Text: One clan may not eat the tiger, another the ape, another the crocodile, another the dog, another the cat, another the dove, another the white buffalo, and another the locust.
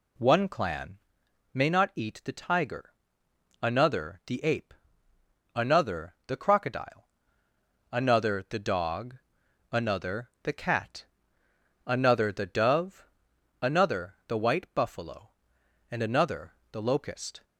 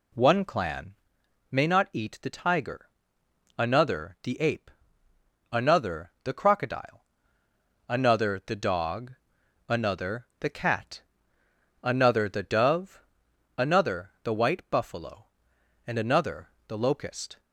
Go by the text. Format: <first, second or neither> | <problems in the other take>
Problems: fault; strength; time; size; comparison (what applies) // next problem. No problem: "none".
neither | pauses between "clan" and "may"; noticeable; the same in both // pauses between "another" and "the"; slight; the same in both